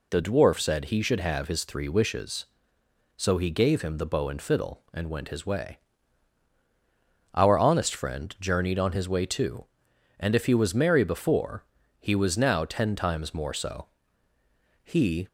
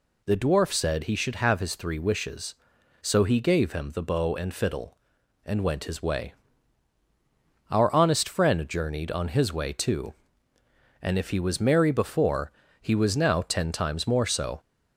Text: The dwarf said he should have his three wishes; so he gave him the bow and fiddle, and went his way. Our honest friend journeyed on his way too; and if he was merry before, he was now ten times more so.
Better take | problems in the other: second | goes on to say "He"; slight; from 14.8 s on; 0.42 s long

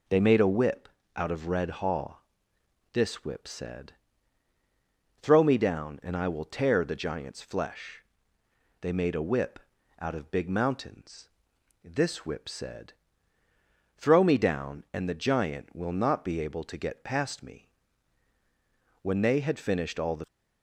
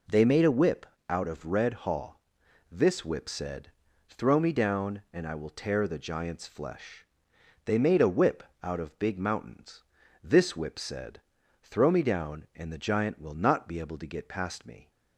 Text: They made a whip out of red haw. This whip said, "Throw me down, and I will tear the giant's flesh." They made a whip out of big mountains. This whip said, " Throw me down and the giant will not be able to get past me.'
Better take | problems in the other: second | pauses between "whip" and "out"; slight; at 0.8 s; 0.28 s long; slight in the second // pauses between "whip" and "out"; at 9.5 s; 0.40 s long; slight in the second // goes on to say "When they had finished all the"; noticeable; from 19.0 s on; 1.2 s long

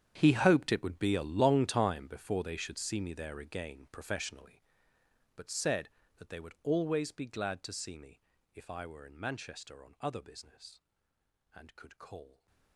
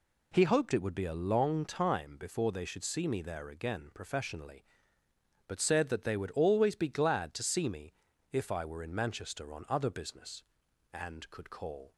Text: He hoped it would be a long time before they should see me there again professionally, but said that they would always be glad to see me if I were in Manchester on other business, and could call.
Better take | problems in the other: second | gets quieter; strong; throughout; 19 dB // pauses between "me" and "if"; slight; at 8.2 s; 0.34 s long; also in the second

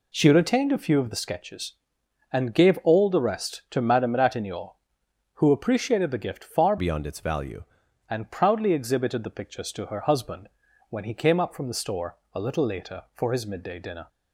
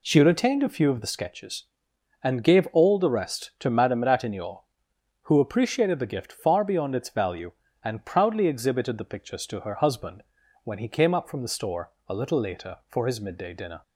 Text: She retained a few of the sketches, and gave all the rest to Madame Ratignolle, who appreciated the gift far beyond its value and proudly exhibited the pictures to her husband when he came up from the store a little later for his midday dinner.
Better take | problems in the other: second | changes voice from "beyond" to "value"; from 6.7 to 7.6 s; 0.9 s long // pauses between "husband" and "when"; at 10.4 s; 0.42 s long; also in the second // pauses between "store" and "a"; slight; at 12.1 s; 0.16 s long; slight in the second

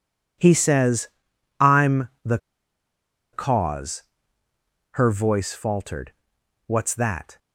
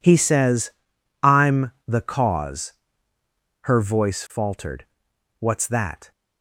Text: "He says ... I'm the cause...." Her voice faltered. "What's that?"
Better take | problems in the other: second | pauses between "I'm" and "the"; slight; at 2.0 s; 0.16 s long; slight in the second // pauses between "the" and "cause"; noticeable; at 2.3 s; 0.95 s long

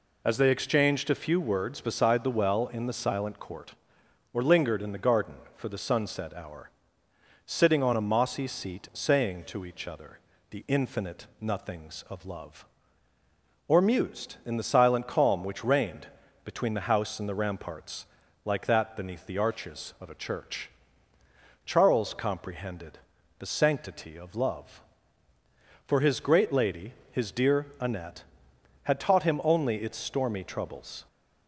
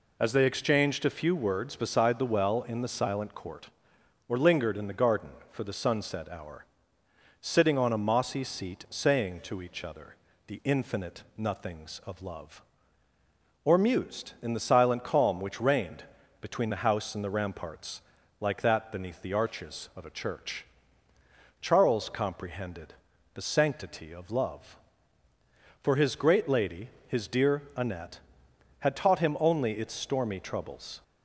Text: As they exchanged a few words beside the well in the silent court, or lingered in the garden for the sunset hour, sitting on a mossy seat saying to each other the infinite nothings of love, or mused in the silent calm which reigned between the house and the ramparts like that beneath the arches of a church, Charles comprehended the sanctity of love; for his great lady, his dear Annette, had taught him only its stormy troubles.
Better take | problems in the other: neither | pauses between "other" and "the"; slight; the same in both // pauses between "reigned" and "between"; slight; the same in both // pauses between "ramparts" and "like"; the same in both // pauses between "comprehended" and "the"; the same in both

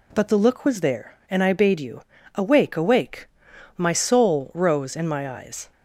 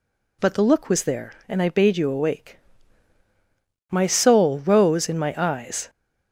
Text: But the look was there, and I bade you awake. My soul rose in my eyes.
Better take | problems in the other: second | pauses between "you" and "awake"; slight; at 2.0 s; 0.34 s long // says "awake" twice; at 2.7 s

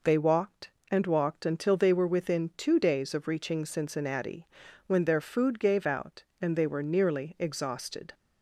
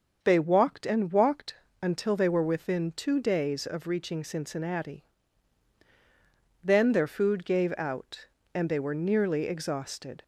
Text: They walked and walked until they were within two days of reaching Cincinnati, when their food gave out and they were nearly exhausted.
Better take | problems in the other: first | starts louder than the rest; until 1.2 s; 6.5 dB // pauses between "walked" and "until"; slight; at 1.5 s; 0.26 s long // says "then" for "when"; at 6.6 s

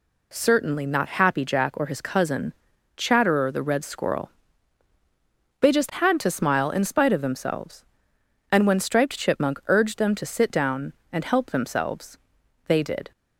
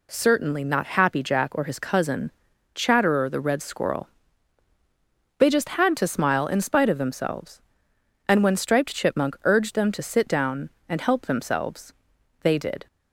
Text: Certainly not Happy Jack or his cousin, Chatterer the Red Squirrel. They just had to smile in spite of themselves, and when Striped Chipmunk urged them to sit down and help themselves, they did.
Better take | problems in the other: neither | none

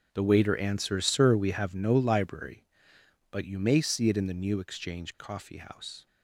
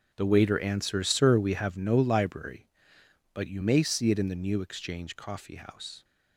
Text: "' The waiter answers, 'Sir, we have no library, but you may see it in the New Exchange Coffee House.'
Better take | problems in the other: neither | starts louder than the rest; the same in both

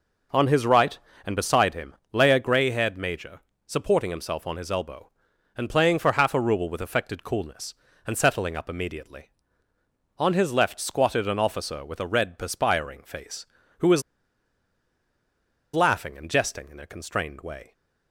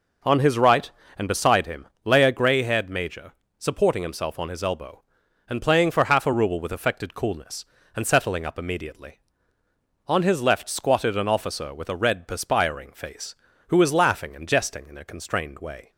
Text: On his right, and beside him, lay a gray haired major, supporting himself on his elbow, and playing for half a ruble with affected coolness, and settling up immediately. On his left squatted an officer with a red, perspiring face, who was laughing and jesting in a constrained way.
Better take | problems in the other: second | pauses between "was" and "laughing"; strong; at 14.0 s; 1.7 s long

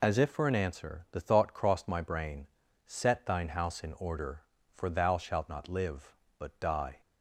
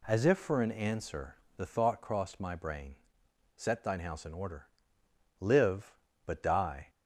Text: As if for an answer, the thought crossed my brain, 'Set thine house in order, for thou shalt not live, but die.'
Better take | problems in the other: first | skips "for thou shalt not"; at 5.0 s

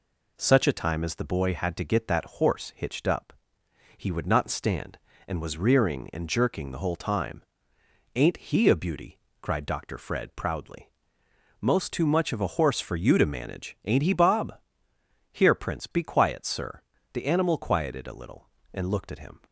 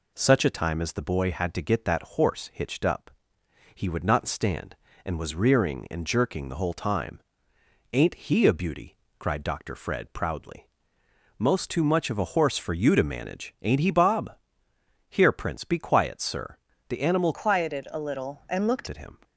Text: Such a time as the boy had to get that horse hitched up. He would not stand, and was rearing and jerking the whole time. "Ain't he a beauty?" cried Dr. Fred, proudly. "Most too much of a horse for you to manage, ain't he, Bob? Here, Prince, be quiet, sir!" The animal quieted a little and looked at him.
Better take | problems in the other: first | changes voice from "quieted" to "looked"; from 17.3 to 18.8 s; 1.5 s long

